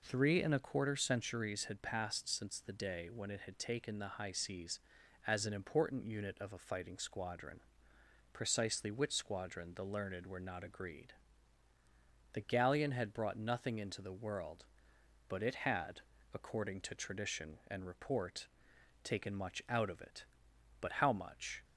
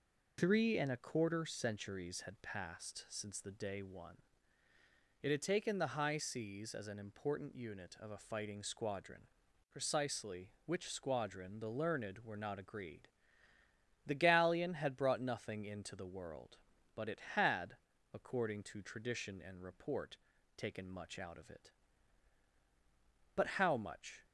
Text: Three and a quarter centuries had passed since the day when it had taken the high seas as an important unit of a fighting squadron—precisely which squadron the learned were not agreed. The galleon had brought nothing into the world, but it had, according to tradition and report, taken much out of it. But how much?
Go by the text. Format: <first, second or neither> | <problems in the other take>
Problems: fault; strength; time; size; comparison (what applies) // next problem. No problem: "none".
first | says "one" for "when"; at 3.8 s